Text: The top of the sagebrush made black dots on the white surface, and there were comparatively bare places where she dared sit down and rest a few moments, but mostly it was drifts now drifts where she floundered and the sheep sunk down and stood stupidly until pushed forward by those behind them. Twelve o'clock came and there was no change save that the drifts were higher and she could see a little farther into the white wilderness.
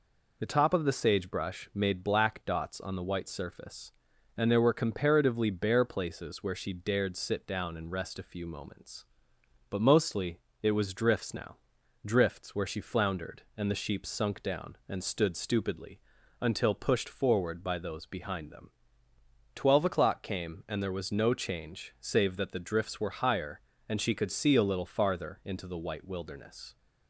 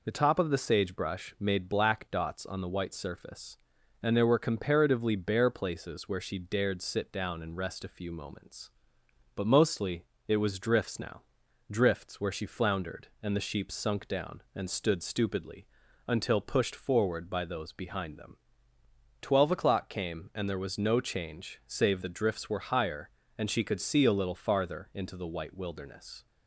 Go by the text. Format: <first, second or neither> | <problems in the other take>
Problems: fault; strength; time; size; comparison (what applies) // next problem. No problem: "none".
first | pauses between "mostly" and "it"; slight; at 10.0 s; 0.24 s long; slight in the first // pauses between "now" and "drifts"; noticeable; at 11.2 s; 0.50 s long; noticeable in the first // pauses between "stupidly" and "until"; at 15.6 s; 0.40 s long; also in the first // skips "that"; at 22.0 s